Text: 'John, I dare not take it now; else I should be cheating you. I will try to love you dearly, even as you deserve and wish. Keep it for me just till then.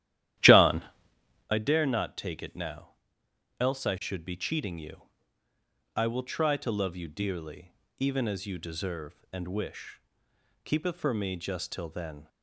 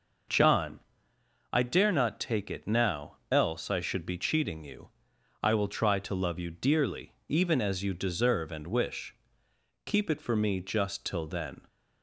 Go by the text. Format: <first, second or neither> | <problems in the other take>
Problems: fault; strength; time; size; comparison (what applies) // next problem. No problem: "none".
second | starts louder than the rest; strong; until 1.6 s; 12.5 dB